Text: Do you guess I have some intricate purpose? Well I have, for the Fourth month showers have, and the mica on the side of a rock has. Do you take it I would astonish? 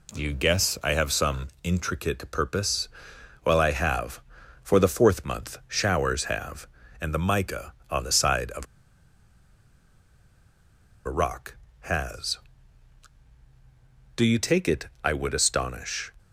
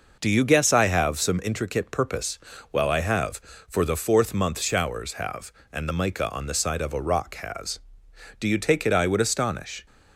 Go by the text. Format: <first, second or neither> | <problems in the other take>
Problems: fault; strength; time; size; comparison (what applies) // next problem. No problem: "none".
second | pauses between "of" and "a"; strong; at 8.6 s; 2.4 s long // pauses between "it" and "I"; slight; at 14.8 s; 0.16 s long